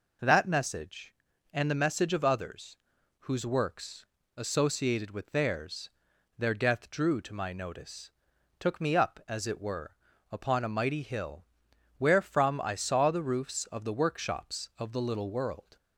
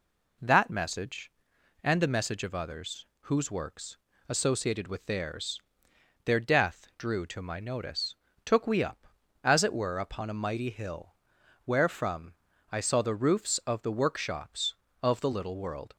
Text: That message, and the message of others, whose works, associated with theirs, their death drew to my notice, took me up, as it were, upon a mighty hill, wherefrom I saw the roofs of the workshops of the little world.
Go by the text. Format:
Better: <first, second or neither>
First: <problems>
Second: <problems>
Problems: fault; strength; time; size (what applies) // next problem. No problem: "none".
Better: first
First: none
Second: says "we" for "me"; at 8.6 s // pauses between "wherefrom" and "I"; at 12.3 s; 0.38 s long